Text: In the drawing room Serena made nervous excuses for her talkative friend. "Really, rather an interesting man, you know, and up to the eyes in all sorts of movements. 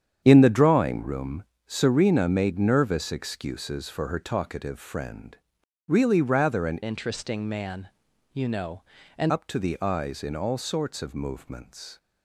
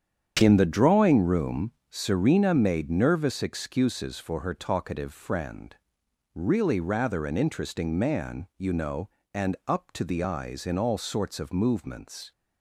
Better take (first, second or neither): second